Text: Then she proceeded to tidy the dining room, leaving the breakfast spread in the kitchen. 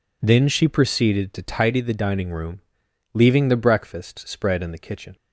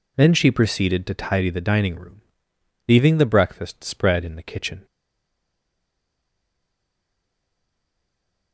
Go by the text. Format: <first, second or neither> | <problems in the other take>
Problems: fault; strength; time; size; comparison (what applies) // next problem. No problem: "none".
first | stays silent after the last word; strong; from 4.8 s on; 3.7 s long